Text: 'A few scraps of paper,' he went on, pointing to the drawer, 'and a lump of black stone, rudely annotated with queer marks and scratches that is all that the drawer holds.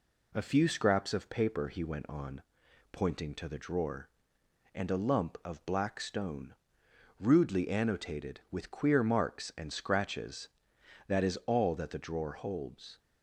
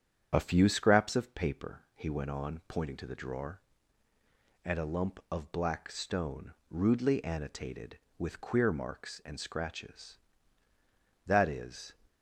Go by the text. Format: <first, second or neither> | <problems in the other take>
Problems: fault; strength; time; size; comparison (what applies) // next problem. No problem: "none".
first | starts louder than the rest; strong; until 1.3 s; 8.5 dB // stops before "all that the drawer holds"; at 12.0 s